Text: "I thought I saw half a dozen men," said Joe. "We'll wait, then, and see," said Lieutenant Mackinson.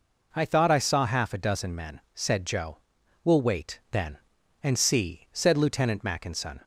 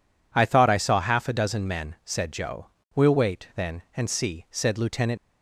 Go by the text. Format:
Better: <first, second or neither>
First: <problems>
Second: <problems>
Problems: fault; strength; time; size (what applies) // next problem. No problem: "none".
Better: first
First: none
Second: stops before "Mackinson"; at 5.1 s